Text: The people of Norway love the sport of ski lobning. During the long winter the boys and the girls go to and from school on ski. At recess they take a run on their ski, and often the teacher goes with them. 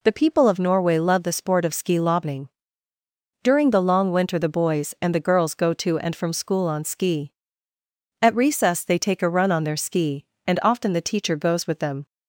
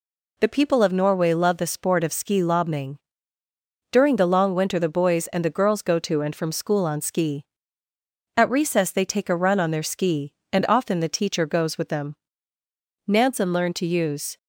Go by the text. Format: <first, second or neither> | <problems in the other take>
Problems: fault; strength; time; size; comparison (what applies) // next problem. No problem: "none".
first | goes on to say "Nansen learned to use"; noticeable; from 13.0 s on; 1.3 s long